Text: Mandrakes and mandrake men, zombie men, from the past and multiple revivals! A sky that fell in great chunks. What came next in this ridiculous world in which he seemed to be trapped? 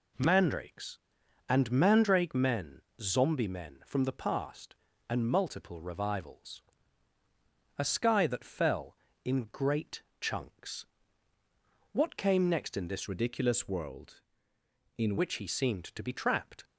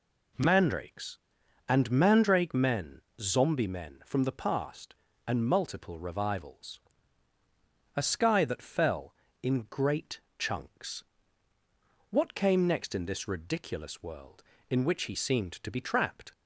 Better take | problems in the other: second | pauses between "great" and "chunks"; slight; at 10.0 s; 0.18 s long; slight in the second // changes voice from "ridiculous" to "in"; from 13.0 to 15.1 s; 2.1 s long

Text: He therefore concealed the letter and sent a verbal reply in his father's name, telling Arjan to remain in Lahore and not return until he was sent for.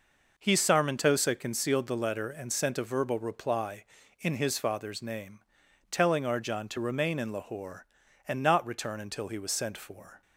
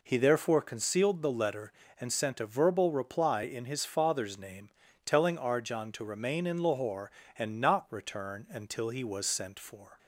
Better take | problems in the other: second | says "sarmentosa" for "therefore"; at 0.5 s

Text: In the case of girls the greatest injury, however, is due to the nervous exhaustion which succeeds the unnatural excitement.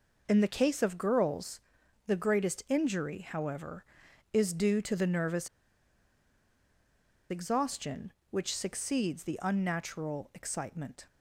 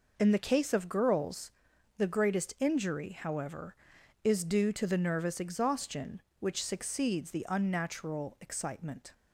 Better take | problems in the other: second | pauses between "girls" and "the"; noticeable; at 1.6 s; 0.46 s long; noticeable in the second // pauses between "nervous" and "exhaustion"; strong; at 5.4 s; 1.8 s long

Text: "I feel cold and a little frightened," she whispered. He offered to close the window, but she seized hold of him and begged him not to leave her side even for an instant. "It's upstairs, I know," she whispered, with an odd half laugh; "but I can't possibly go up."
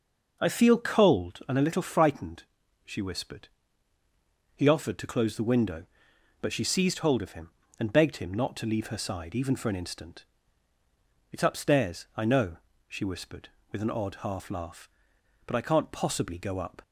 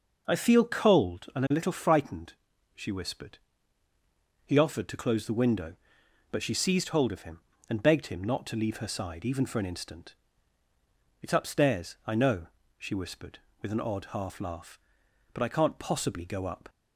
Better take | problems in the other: neither | none

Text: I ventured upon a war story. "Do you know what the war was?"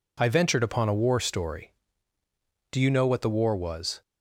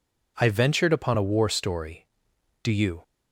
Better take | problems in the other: first | stops before "know what the war was"; at 3.0 s

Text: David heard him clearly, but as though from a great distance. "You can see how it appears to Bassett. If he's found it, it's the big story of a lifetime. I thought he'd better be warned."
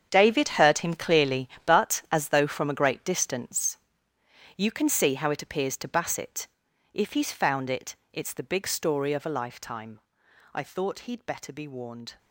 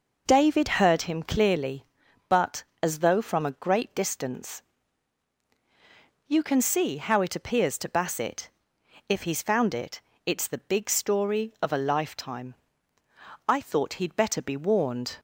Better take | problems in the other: second | gets quieter; strong; throughout; 14 dB

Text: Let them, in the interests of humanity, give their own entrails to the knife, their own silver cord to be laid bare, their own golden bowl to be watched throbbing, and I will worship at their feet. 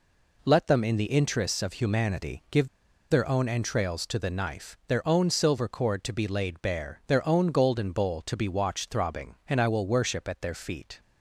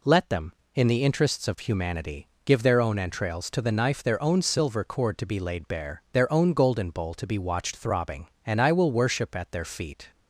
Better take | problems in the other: second | pauses between "give" and "their"; at 2.6 s; 0.44 s long

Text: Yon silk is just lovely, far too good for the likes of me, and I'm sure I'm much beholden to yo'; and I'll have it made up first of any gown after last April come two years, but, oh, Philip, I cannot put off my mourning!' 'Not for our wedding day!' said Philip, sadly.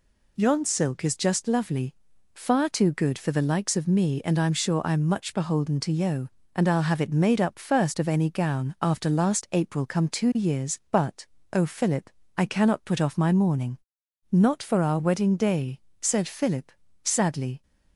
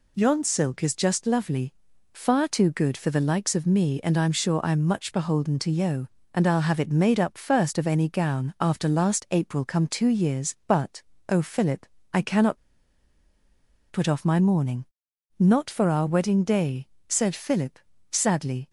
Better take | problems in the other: first | pauses between "cannot" and "put"; strong; at 12.5 s; 1.3 s long

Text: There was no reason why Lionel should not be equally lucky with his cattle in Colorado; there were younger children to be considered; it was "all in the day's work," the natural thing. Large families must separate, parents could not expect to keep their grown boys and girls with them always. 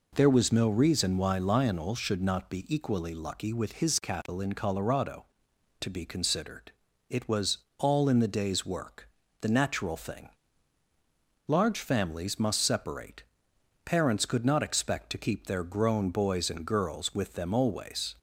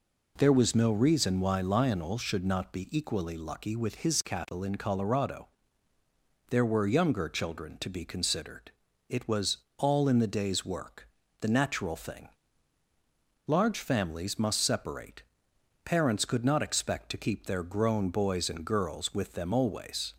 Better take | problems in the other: second | skips "there were younger children"; at 5.5 s // pauses between "was" and "all"; slight; at 7.5 s; 0.22 s long; slight in the second

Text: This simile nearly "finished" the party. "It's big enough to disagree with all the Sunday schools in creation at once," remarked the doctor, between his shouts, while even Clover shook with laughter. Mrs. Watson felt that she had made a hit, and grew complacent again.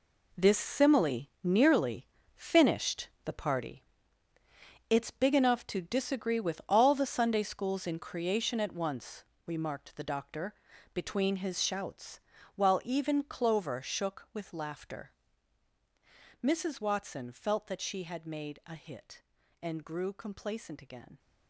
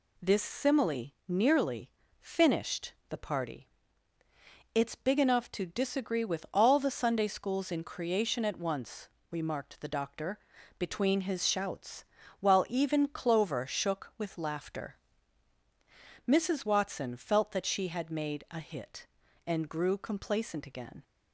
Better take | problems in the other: second | gets quieter; strong; throughout; 11.5 dB // pauses between "simile" and "nearly"; slight; at 1.2 s; 0.16 s long; slight in the second // pauses between "nearly" and "finished"; slight; at 2.0 s; 0.28 s long; slight in the second // pauses between "finished" and "the"; slight; at 3.0 s; 0.16 s long; slight in the second

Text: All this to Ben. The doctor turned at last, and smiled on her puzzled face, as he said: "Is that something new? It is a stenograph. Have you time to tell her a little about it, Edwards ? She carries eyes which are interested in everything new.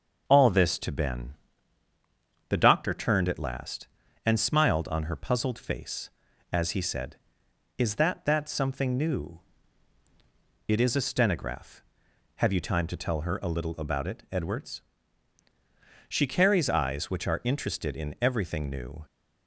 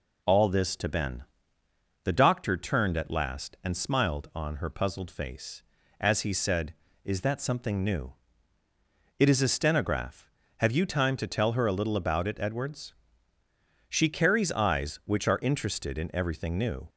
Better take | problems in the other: second | starts louder than the rest; until 1.2 s; 6.5 dB // says "that" twice; at 8.2 s

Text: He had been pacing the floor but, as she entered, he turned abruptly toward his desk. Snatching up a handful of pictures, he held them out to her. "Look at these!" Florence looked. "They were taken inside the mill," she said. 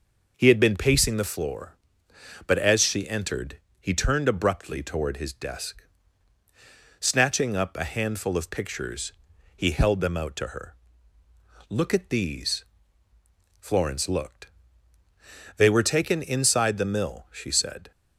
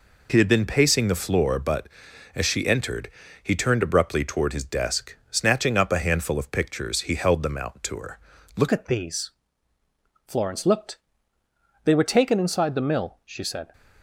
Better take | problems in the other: first | changes voice at "at"; from 8.7 s on; 5.0 s long

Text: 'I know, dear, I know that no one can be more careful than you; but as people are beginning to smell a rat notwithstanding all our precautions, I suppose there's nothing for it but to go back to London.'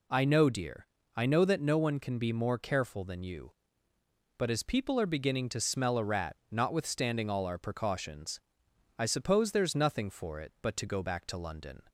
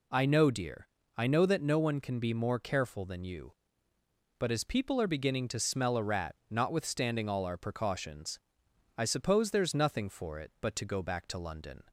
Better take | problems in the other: neither | pauses between "rat" and "notwithstanding"; slight; the same in both

